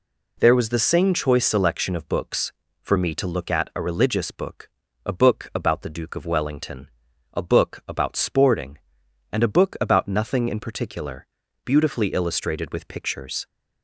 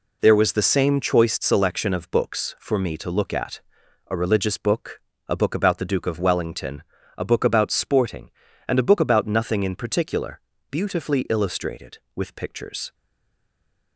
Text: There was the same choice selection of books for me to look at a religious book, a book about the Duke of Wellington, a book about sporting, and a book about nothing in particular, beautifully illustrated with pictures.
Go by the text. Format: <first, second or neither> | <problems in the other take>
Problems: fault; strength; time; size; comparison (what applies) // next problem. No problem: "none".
first | pauses between "at" and "a"; noticeable; at 3.5 s; 0.48 s long // stays silent after the last word; from 12.9 s on; 1.0 s long